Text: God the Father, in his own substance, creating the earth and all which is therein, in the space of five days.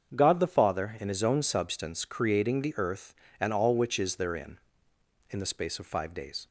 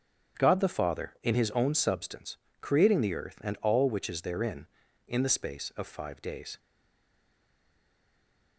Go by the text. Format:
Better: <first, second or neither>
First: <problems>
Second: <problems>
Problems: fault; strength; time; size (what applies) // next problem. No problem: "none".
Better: first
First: starts louder than the rest; until 1.1 s; 7 dB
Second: starts louder than the rest; until 1.4 s; 7 dB // stays silent after the last word; noticeable; from 6.5 s on; 2.0 s long